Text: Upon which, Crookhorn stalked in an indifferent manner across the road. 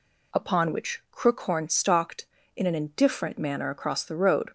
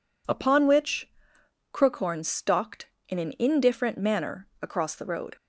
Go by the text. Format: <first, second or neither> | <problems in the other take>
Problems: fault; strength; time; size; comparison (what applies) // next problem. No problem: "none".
neither | none